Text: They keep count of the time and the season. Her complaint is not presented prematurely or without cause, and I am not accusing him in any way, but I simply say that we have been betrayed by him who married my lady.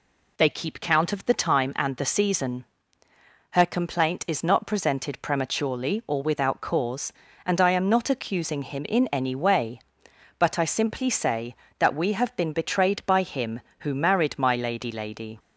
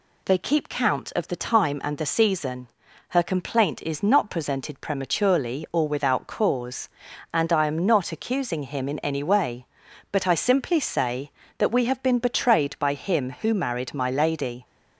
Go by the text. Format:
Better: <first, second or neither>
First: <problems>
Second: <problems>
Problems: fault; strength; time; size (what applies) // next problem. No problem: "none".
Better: second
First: says "lady" twice; at 14.8 s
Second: none